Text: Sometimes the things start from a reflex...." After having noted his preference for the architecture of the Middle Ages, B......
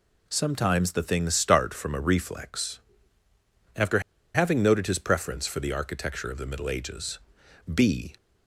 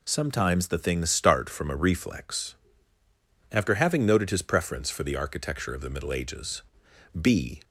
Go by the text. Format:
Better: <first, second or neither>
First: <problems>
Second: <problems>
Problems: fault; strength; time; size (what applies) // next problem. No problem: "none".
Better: second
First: pauses between "After" and "having"; slight; at 3.9 s; 0.34 s long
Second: none